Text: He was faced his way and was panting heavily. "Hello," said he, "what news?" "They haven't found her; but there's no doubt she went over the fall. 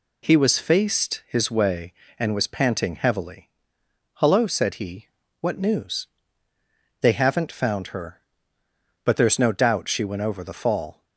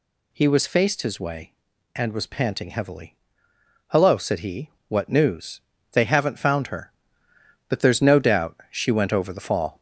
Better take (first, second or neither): first